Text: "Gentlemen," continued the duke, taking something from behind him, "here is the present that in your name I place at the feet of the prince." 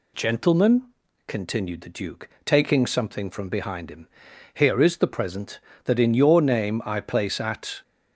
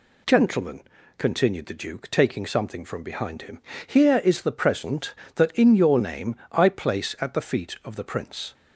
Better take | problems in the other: second | stops before "the feet of the prince"; at 7.8 s

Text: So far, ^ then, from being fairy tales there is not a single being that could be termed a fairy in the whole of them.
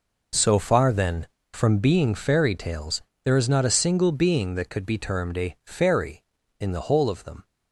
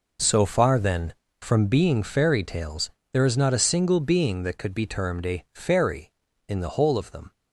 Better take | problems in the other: neither | pauses between "tales" and "there"; slight; the same in both

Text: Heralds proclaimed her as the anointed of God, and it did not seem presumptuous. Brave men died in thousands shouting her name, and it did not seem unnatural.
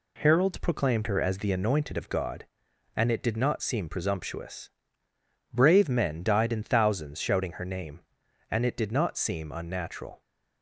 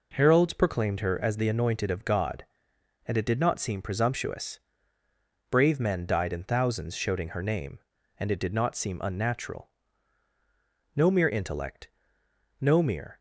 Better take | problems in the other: first | goes on to say "No mere intellect no mere"; strong; from 10.9 s on; 2.2 s long

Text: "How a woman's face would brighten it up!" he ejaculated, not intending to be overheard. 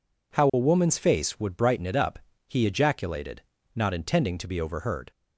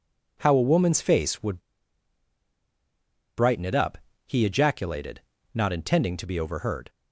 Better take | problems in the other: first | pauses between "would" and "brighten"; strong; at 1.6 s; 1.7 s long

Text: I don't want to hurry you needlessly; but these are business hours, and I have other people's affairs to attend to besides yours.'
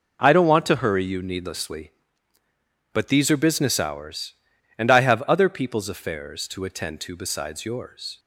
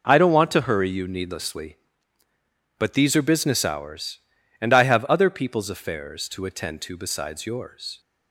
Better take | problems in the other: neither | none

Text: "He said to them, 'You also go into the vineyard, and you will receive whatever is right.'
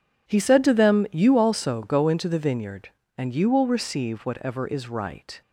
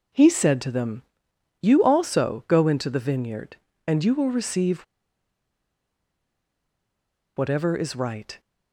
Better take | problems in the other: first | pauses between "receive" and "whatever"; strong; at 4.8 s; 2.5 s long

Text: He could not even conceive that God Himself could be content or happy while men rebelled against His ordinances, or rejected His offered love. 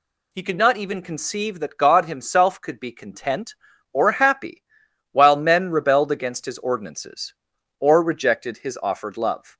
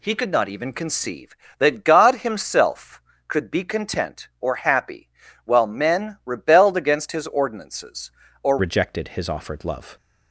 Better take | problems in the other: first | pauses between "happy" and "while"; at 5.0 s; 0.38 s long; noticeable in the first // changes voice at "rejected"; from 8.5 s on; 1.4 s long

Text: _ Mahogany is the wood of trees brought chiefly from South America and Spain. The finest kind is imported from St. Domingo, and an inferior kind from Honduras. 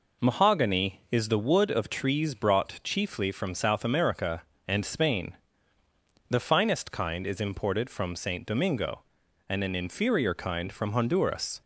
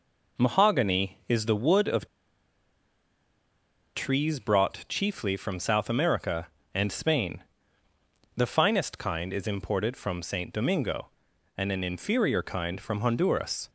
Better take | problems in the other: first | pauses between "of" and "trees"; strong; at 2.0 s; 1.8 s long

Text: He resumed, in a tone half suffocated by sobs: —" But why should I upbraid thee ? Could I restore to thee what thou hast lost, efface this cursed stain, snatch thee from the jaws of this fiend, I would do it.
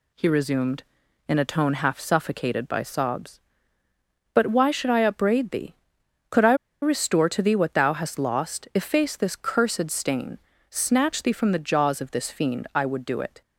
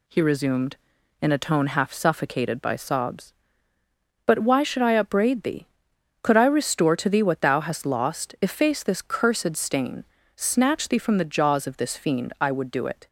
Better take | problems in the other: second | pauses between "I" and "restore"; slight; at 6.5 s; 0.28 s long

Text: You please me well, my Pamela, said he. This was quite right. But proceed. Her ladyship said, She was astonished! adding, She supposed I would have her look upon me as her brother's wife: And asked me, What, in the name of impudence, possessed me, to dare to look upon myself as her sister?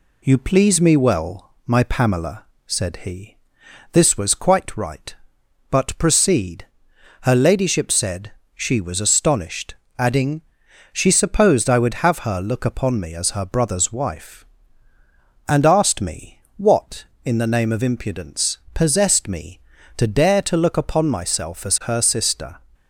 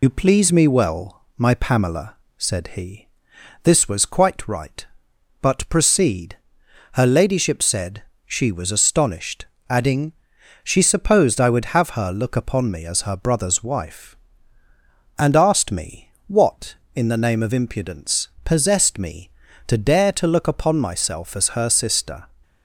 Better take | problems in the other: first | loses the start of "You"; at 0.0 s; 65 ms

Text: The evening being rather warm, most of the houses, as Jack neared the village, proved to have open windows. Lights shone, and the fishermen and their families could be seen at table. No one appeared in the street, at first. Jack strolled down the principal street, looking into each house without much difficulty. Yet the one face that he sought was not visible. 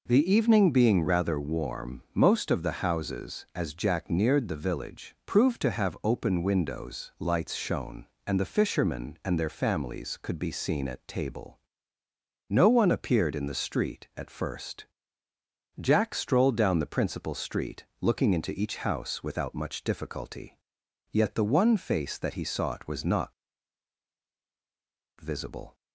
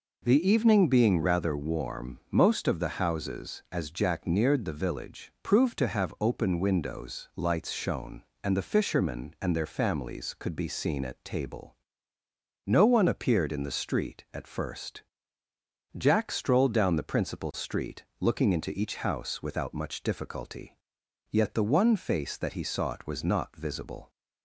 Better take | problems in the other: second | pauses between "not" and "visible"; strong; at 23.3 s; 1.8 s long

